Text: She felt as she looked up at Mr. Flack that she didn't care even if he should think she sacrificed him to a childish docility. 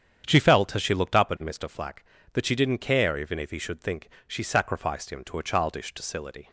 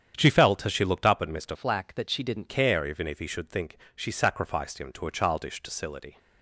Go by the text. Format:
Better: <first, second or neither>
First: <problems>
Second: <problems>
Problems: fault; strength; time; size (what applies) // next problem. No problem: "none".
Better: first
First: starts louder than the rest; strong; until 1.2 s; 8.5 dB // pauses between "think" and "she"; slight; at 4.0 s; 0.18 s long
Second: starts louder than the rest; strong; until 1.2 s; 8.5 dB // changes voice from "Flack" to "didn't"; from 1.5 to 2.4 s; 0.9 s long // pauses between "think" and "she"; slight; at 3.7 s; 0.18 s long